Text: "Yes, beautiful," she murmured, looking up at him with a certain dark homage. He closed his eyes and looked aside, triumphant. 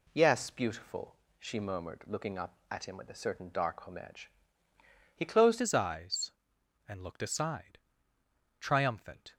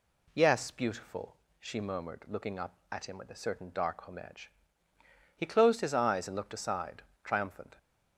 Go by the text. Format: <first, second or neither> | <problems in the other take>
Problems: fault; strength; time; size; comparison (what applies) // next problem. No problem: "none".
second | changes voice at "his"; from 5.5 s on; 3.8 s long